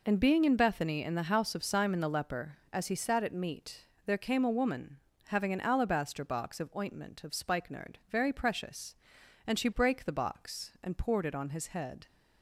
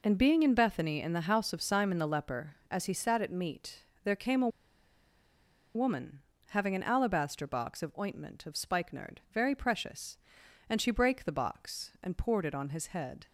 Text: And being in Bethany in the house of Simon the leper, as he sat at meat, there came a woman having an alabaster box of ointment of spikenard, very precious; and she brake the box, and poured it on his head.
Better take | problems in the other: first | pauses between "a" and "woman"; strong; at 4.4 s; 1.2 s long // pauses between "woman" and "having"; slight; at 6.2 s; 0.30 s long; slight in the first

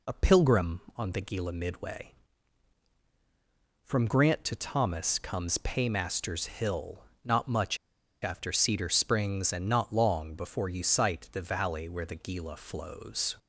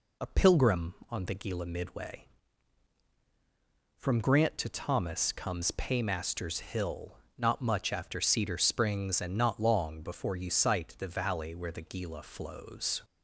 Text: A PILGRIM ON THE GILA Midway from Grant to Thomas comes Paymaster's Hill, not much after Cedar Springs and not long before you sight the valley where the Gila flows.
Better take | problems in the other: second | pauses between "much" and "after"; noticeable; at 7.7 s; 0.46 s long

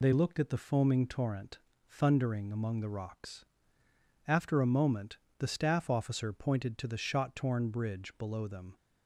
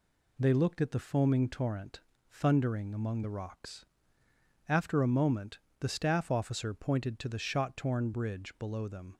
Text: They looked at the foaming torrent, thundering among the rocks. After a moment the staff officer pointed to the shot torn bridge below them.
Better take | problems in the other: second | loses the start of "They"; at 0.0 s; 30 ms // pauses between "moment" and "the"; slight; at 5.1 s; 0.20 s long; slight in the second

